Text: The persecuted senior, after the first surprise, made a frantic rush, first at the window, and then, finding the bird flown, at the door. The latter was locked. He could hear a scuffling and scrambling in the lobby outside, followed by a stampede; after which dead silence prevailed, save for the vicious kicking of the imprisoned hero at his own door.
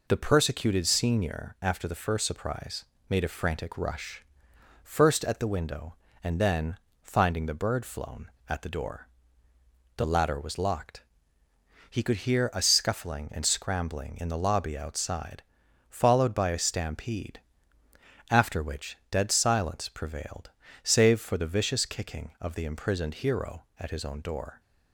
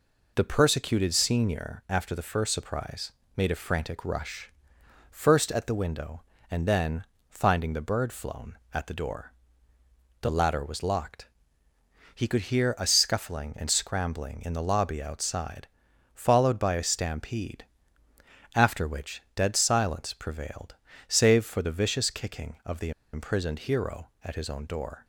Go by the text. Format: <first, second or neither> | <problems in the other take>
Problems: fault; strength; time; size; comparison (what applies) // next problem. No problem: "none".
first | pauses between "the" and "imprisoned"; slight; at 22.9 s; 0.22 s long